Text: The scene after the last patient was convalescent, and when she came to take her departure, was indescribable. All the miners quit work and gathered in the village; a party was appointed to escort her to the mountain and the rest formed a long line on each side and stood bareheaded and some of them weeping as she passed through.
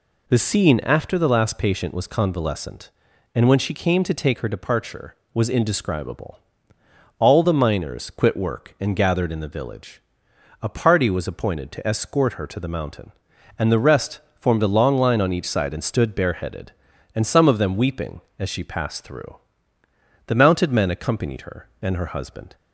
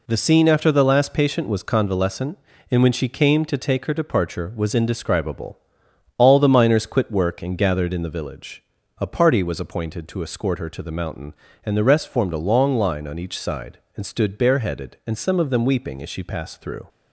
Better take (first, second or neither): second